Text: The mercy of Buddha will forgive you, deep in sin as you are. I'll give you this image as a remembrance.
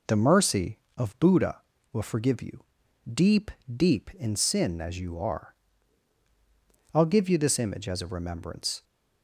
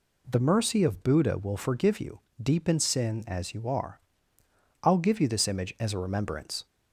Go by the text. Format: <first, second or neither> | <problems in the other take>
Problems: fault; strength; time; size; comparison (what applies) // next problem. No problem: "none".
second | says "deep" twice; at 3.7 s